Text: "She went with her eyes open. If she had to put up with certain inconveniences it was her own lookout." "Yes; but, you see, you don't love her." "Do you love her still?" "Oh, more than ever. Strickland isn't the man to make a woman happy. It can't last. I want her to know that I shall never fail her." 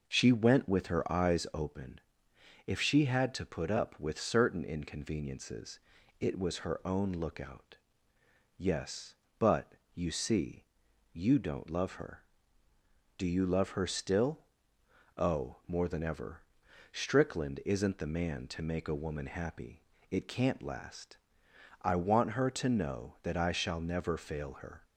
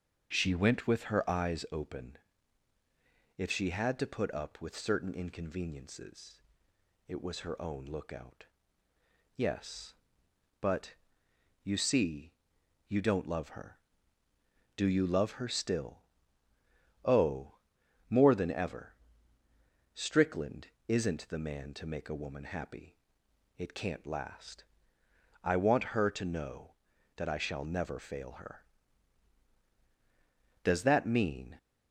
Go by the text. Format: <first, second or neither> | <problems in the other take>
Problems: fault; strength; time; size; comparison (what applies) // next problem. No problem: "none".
first | starts louder than the rest; until 1.3 s; 6 dB // pauses between "inconveniences" and "it"; noticeable; at 6.3 s; 0.66 s long; also in the first // pauses between "Strickland" and "isn't"; slight; at 20.6 s; 0.18 s long // goes on to say "Does that mean"; noticeable; from 30.6 s on; 0.94 s long